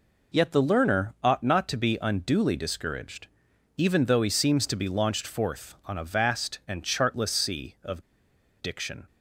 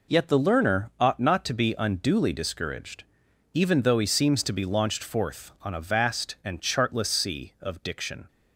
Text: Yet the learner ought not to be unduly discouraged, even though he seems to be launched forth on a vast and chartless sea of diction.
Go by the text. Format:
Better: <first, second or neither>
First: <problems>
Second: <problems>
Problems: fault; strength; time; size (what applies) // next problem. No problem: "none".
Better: second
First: pauses between "of" and "diction"; noticeable; at 8.0 s; 0.60 s long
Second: none